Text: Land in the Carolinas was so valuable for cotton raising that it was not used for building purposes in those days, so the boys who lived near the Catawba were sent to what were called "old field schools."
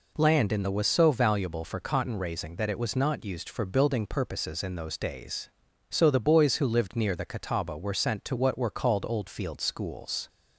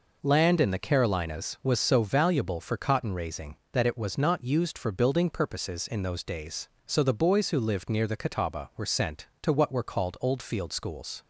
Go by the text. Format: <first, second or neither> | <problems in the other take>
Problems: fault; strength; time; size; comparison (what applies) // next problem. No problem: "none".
second | skips "Carolinas"; at 0.7 s